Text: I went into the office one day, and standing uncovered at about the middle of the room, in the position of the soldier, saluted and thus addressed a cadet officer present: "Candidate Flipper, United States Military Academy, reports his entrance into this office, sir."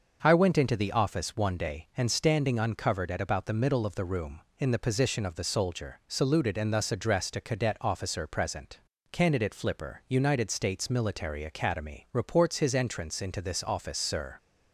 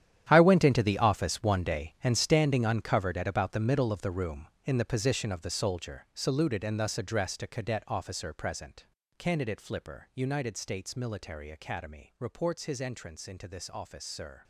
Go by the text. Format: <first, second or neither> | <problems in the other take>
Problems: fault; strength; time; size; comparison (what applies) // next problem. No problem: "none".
first | gets quieter; strong; throughout; 15 dB // starts louder than the rest; strong; until 1.3 s; 11 dB; also in the first